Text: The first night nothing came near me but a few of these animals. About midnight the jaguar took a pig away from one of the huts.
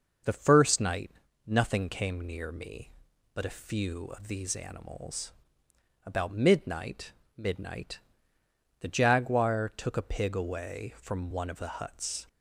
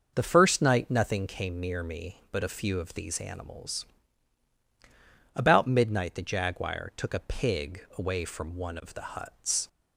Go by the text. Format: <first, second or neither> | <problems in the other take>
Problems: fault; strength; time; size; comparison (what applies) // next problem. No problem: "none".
second | starts louder than the rest; noticeable; until 1.6 s; 6 dB; noticeable in the second // pauses between "night" and "nothing"; slight; at 1.0 s; 0.36 s long // says "midnight" twice; at 7.3 s